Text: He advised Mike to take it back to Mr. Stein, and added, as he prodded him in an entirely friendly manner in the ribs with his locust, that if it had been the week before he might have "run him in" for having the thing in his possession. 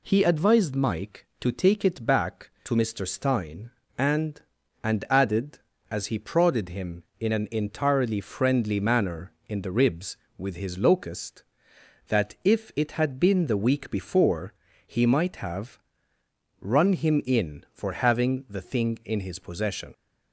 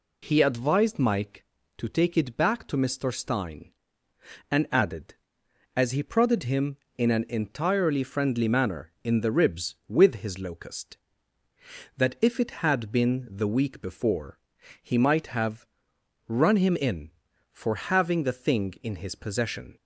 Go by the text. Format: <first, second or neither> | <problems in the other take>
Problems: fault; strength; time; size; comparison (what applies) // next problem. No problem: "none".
second | says "and" twice; at 4.8 s // pauses between "before" and "he"; slight; at 14.5 s; 0.34 s long; also in the second // pauses between "have" and "run"; noticeable; at 15.7 s; 0.82 s long; noticeable in the second